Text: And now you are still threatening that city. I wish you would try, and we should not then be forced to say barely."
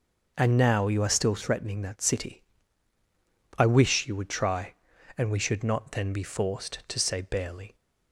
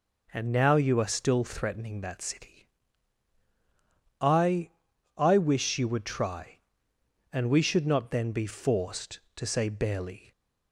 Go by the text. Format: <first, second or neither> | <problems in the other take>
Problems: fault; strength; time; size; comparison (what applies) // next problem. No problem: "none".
first | says "I" twice; at 5.1 s